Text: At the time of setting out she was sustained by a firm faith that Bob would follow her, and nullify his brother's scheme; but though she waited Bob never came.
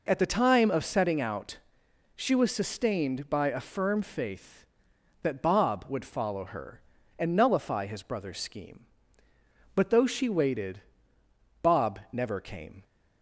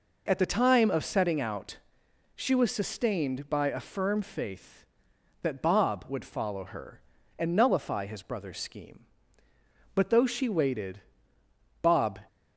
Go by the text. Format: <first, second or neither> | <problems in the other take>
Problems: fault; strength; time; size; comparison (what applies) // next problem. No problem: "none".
first | pauses between "out" and "she"; noticeable; at 1.7 s; 0.58 s long; noticeable in the first // pauses between "waited" and "Bob"; noticeable; at 10.9 s; 0.82 s long; noticeable in the first // stops before "never came"; at 12.2 s